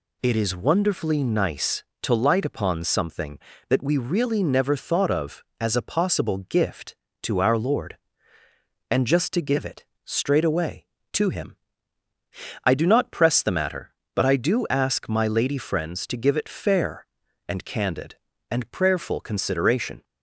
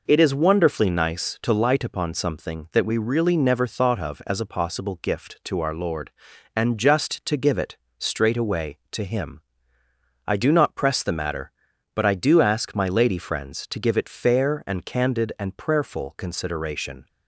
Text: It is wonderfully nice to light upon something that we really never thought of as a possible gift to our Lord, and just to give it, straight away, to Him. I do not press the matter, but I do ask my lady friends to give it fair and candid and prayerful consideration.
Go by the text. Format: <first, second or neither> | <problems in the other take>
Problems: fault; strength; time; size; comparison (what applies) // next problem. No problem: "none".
neither | none